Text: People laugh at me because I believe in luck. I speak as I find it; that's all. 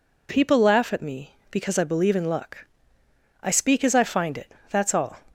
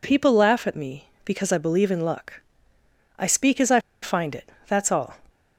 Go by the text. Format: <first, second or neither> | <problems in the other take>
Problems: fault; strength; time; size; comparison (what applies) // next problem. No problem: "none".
first | pauses between "I" and "find"; slight; at 3.7 s; 0.22 s long